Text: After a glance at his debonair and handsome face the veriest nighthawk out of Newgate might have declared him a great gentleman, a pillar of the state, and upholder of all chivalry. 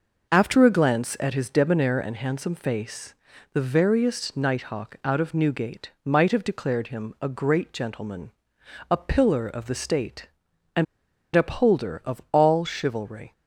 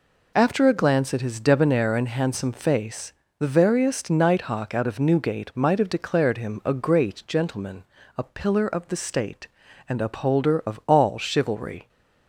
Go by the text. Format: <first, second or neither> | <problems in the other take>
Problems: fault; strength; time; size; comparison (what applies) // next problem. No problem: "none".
second | pauses between "face" and "the"; at 3.1 s; 0.40 s long; slight in the second // pauses between "and" and "upholder"; noticeable; at 10.8 s; 0.48 s long